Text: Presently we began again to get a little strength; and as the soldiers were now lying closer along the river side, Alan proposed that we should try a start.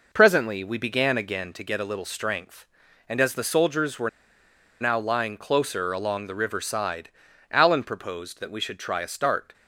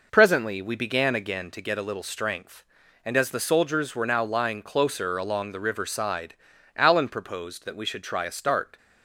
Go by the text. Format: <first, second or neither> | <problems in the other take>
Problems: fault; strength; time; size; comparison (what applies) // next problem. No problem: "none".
second | pauses between "were" and "now"; noticeable; at 4.0 s; 0.71 s long